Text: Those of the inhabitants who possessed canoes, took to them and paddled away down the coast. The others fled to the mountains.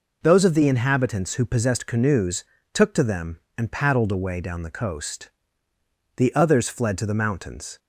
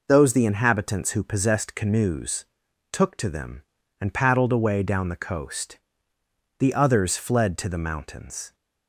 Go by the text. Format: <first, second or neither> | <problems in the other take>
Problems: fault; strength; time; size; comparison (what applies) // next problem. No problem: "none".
first | skips "of"; at 0.3 s